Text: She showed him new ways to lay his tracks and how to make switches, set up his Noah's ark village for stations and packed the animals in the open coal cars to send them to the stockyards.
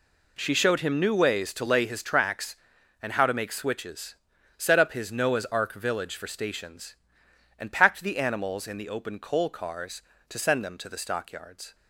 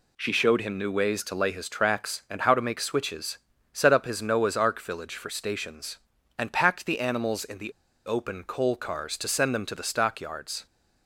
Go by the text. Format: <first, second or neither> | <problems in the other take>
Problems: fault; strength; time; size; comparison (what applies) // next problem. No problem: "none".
first | pauses between "the" and "open"; slight; at 7.7 s; 0.33 s long